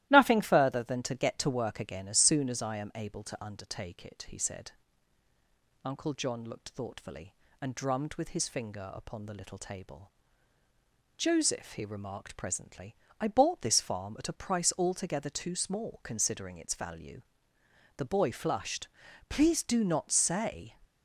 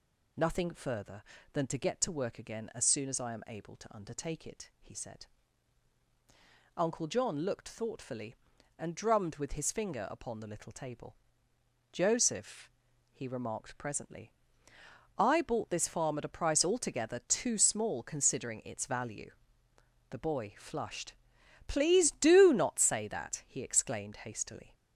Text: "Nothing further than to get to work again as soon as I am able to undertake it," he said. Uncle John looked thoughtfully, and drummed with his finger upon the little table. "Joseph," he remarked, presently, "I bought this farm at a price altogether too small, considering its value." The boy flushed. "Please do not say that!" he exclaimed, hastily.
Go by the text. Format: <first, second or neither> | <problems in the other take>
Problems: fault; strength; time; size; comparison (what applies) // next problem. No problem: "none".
second | starts louder than the rest; strong; until 1.1 s; 15 dB // stops before "that he exclaimed hastily"; at 20.8 s